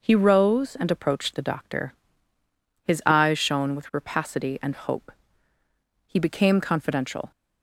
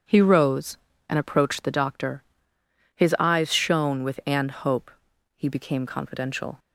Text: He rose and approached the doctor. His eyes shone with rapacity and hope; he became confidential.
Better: first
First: none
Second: skips "rapacity"; at 4.2 s

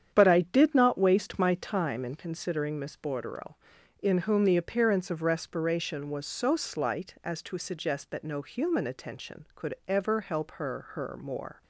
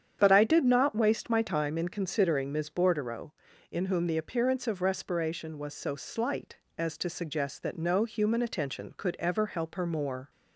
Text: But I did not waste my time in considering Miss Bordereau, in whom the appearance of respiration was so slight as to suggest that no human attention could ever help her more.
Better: second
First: starts louder than the rest; strong; until 1.1 s; 8.5 dB // says "her" twice; at 10.9 s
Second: starts louder than the rest; strong; until 1.2 s; 8.5 dB

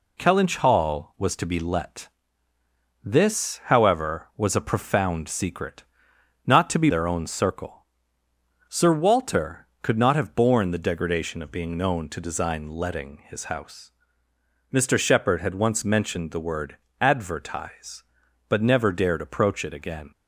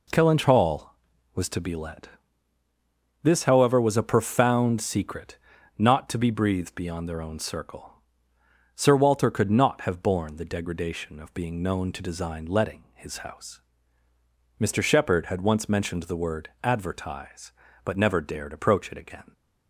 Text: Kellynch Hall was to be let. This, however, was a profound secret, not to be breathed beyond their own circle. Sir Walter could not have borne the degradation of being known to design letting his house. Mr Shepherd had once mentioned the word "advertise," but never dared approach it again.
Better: second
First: skips "breathed beyond"; at 6.8 s // pauses between "word" and "advertise"; slight; at 16.7 s; 0.24 s long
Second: none

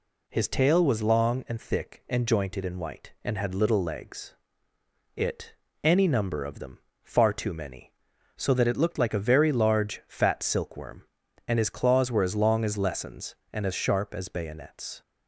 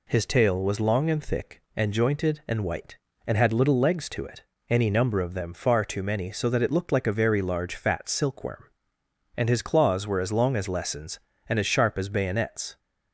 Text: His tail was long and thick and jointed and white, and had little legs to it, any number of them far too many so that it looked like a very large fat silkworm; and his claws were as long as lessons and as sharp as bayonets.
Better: second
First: skips "to"; at 4.7 s // pauses between "them" and "far"; slight; at 6.7 s; 0.24 s long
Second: none

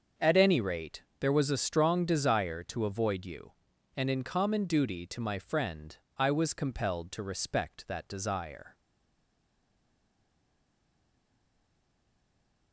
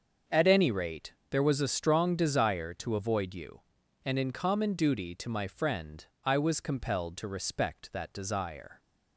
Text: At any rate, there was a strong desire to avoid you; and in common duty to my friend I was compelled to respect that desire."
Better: second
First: starts louder than the rest; until 1.3 s; 6.5 dB // pauses between "friend" and "I"; slight; at 5.9 s; 0.23 s long // stays silent after the last word; strong; from 8.7 s on; 4.0 s long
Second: starts louder than the rest; until 1.4 s; 6.5 dB // pauses between "friend" and "I"; slight; at 6.0 s; 0.22 s long

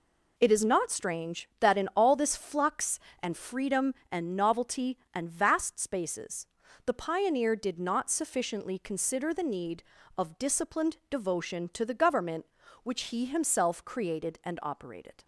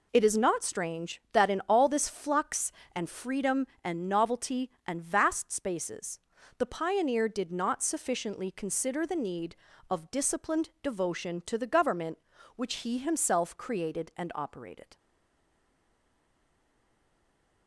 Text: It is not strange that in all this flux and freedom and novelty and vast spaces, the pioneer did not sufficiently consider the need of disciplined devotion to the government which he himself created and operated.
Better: first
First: none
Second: stays silent after the last word; strong; from 14.9 s on; 2.7 s long

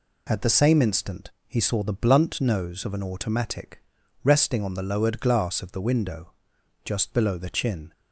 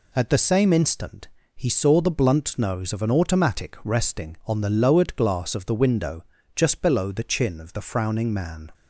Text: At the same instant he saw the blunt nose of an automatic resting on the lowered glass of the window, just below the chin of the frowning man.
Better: second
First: pauses between "instant" and "he"; slight; at 1.2 s; 0.18 s long // pauses between "automatic" and "resting"; at 3.7 s; 0.44 s long // stops before "of the frowning man"; at 7.9 s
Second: pauses between "instant" and "he"; slight; at 1.2 s; 0.28 s long

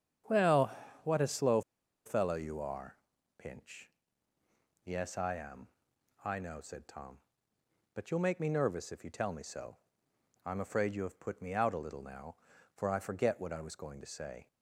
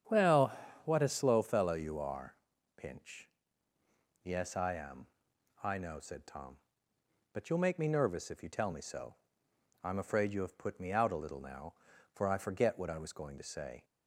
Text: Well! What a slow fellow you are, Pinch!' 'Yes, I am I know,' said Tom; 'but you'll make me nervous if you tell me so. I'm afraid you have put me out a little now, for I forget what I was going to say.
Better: second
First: starts louder than the rest; strong; until 1.5 s; 9 dB // pauses between "slow" and "fellow"; at 1.6 s; 0.44 s long // pauses between "am" and "I"; noticeable; at 5.6 s; 0.56 s long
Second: starts louder than the rest; strong; until 1.4 s; 9 dB // pauses between "am" and "I"; noticeable; at 5.0 s; 0.56 s long

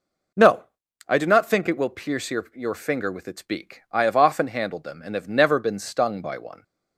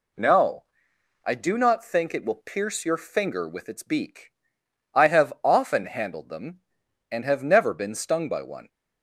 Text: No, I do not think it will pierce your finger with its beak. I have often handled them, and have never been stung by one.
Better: second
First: says "your" twice; at 2.5 s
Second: none

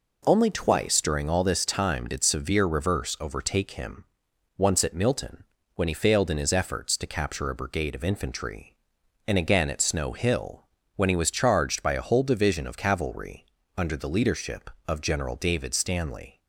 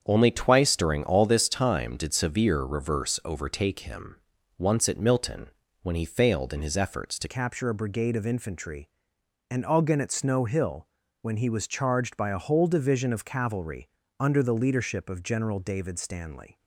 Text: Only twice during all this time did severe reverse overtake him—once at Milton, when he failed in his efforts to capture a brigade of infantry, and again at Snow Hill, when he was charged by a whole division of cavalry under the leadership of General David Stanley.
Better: first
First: pauses between "cavalry" and "under"; slight; at 13.4 s; 0.30 s long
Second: starts louder than the rest; strong; until 1.0 s; 7.5 dB // changes voice at "capture"; from 7.2 s on; 9.3 s long // pauses between "cavalry" and "under"; slight; at 13.8 s; 0.30 s long

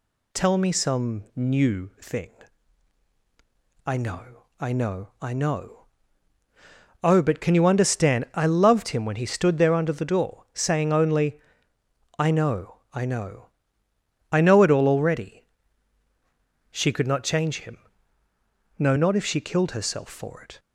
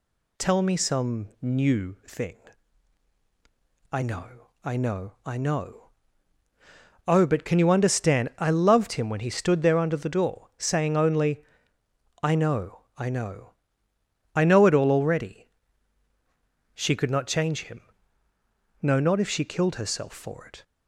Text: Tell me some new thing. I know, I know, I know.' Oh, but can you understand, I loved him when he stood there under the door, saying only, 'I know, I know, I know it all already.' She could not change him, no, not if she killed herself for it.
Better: neither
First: none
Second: none

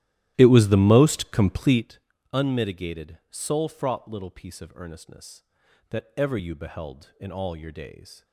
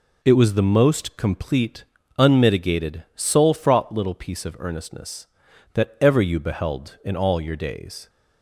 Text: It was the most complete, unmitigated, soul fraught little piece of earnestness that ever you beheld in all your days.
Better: second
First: starts louder than the rest; strong; until 1.9 s; 13.5 dB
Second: none

